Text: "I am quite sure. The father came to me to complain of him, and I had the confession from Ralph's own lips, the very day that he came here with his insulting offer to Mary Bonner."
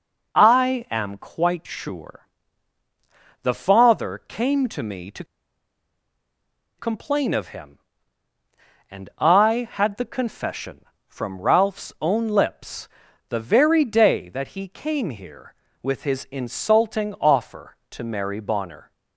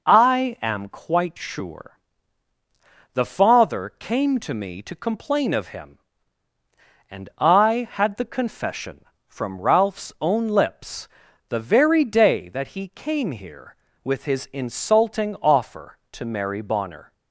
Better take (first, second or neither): second